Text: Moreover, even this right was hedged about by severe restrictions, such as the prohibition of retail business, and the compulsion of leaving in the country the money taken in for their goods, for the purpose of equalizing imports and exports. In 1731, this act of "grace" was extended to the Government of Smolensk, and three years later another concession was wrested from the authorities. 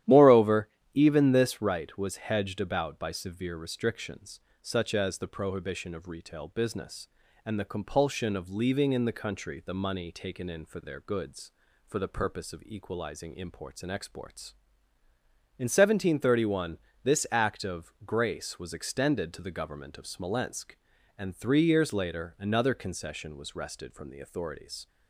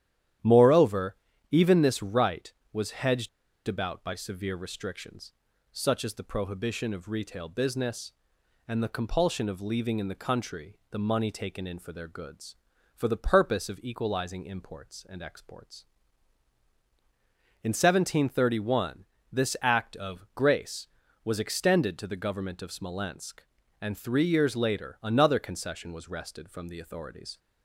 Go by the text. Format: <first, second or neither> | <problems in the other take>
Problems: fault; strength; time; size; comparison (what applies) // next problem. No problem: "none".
first | starts louder than the rest; strong; until 1.7 s; 11 dB; strong in the first // pauses between "hedged" and "about"; at 3.2 s; 0.38 s long